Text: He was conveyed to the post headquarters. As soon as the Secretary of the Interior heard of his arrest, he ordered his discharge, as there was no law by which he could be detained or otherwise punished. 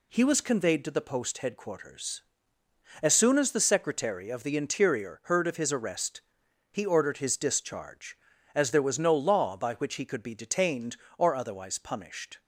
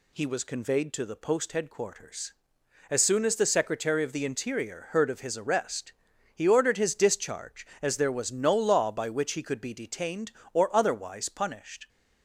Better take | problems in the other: neither | none

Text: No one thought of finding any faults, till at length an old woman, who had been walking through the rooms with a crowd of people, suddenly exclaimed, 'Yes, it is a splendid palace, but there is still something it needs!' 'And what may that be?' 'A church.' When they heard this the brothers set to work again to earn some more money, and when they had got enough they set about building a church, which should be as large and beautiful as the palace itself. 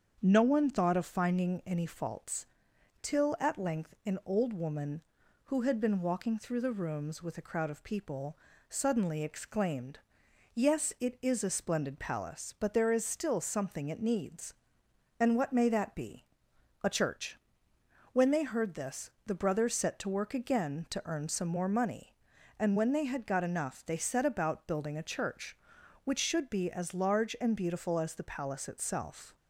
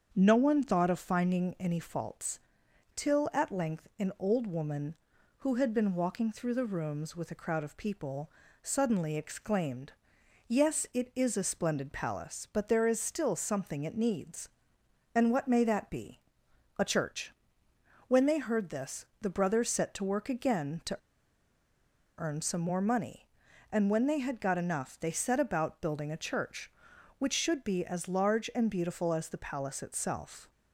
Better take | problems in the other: first | starts louder than the rest; until 1.1 s; 7 dB; also in the first // pauses between "this" and "the"; slight; at 19.0 s; 0.16 s long; slight in the first // pauses between "to" and "earn"; at 20.9 s; 1.2 s long

